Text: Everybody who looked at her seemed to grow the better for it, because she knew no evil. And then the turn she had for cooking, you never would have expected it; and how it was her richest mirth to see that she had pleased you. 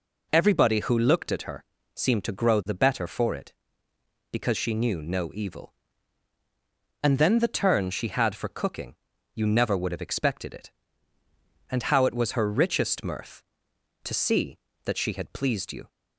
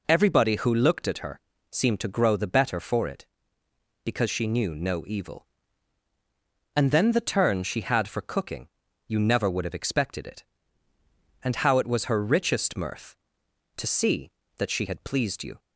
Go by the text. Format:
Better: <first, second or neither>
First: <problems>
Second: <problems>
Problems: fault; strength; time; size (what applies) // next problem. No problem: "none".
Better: neither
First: pauses between "her" and "seemed"; slight; at 1.6 s; 0.32 s long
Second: pauses between "her" and "seemed"; slight; at 1.3 s; 0.32 s long